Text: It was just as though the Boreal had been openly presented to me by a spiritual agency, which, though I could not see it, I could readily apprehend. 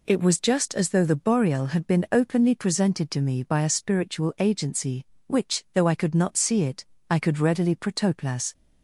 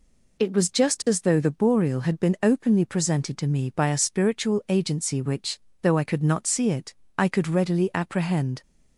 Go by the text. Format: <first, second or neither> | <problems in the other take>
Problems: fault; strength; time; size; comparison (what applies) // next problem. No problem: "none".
second | says "protoplas" for "apprehend"; at 7.7 s